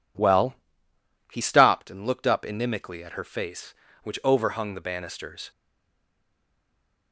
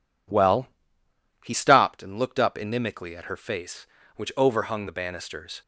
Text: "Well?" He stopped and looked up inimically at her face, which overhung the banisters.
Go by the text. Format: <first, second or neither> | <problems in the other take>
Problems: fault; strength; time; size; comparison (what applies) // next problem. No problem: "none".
second | stays silent after the last word; noticeable; from 5.5 s on; 1.6 s long